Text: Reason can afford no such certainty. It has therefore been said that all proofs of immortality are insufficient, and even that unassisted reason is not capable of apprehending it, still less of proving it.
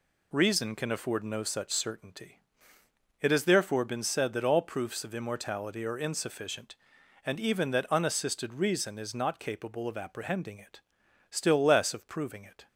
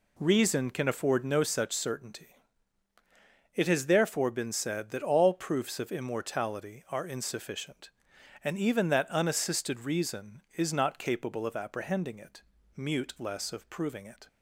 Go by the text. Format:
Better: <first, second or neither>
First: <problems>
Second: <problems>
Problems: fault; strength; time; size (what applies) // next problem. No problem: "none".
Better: first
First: none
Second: says "mute" for "still"; at 12.7 s